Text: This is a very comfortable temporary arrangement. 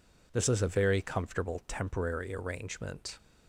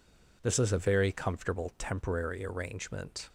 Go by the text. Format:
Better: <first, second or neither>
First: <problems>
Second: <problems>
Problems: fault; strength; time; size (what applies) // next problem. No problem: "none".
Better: neither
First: none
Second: none